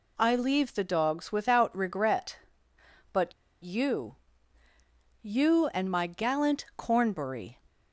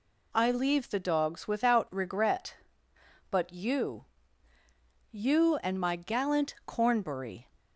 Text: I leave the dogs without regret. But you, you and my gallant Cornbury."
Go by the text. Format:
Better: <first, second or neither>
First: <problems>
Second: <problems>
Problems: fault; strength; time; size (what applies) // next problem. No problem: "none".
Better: second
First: pauses between "But" and "you"; slight; at 3.3 s; 0.30 s long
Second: none